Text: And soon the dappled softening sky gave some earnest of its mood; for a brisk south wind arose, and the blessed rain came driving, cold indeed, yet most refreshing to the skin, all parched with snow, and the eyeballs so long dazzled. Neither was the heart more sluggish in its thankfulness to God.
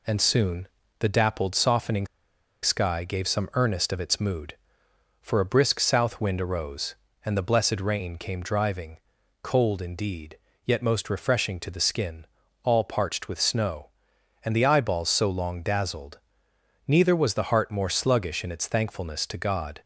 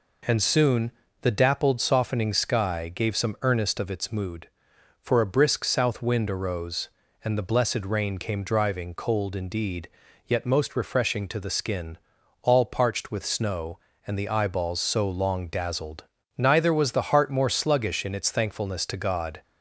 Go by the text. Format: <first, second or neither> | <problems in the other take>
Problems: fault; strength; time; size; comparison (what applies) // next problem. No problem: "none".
second | pauses between "soon" and "the"; slight; at 0.6 s; 0.32 s long; slight in the second // pauses between "softening" and "sky"; noticeable; at 2.0 s; 0.56 s long